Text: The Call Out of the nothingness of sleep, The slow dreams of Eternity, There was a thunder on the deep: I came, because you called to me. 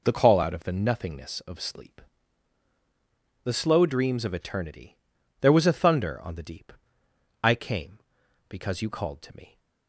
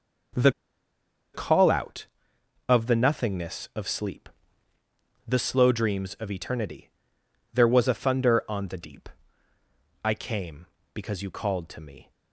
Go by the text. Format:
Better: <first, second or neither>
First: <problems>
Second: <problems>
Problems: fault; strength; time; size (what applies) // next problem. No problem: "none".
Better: first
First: none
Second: starts louder than the rest; noticeable; until 2.7 s; 6 dB // pauses between "The" and "Call"; noticeable; at 0.5 s; 0.83 s long